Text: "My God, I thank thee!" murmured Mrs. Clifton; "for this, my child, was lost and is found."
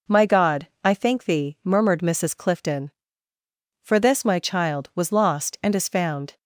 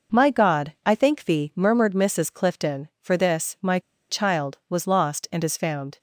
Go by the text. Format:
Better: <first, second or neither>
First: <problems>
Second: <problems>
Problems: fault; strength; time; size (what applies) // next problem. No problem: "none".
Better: first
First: none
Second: pauses between "my" and "child"; slight; at 3.7 s; 0.30 s long